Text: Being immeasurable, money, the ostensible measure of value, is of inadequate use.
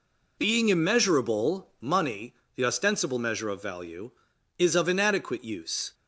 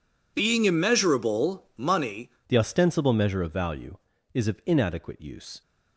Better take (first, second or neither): first